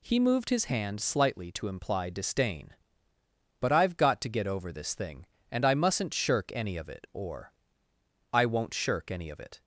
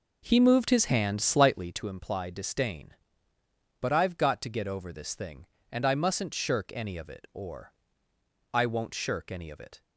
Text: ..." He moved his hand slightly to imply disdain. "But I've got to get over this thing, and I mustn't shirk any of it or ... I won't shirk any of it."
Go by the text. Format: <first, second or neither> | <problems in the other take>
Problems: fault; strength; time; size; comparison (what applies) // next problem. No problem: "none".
first | starts louder than the rest; noticeable; until 1.9 s; 5 dB